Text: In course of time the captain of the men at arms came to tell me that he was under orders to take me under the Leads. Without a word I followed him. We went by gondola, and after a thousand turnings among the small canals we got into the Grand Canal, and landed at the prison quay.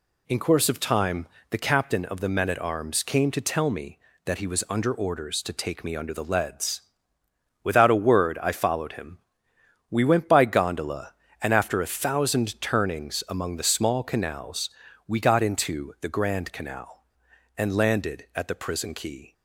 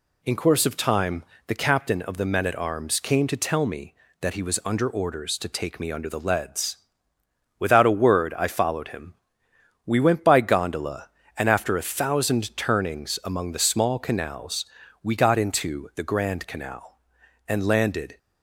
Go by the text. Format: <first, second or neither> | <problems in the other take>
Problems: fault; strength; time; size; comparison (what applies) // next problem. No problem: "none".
first | pauses between "time" and "the"; slight; at 1.2 s; 0.24 s long; slight in the first // pauses between "canals" and "we"; slight; at 14.6 s; 0.36 s long; slight in the first // stops before "at the prison quay"; at 18.1 s